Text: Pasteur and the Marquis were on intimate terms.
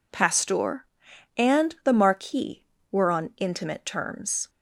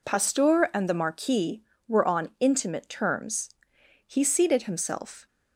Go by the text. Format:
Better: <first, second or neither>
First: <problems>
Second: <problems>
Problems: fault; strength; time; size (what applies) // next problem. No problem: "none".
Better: first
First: none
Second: goes on to say "He seated himself"; noticeable; from 4.0 s on; 1.2 s long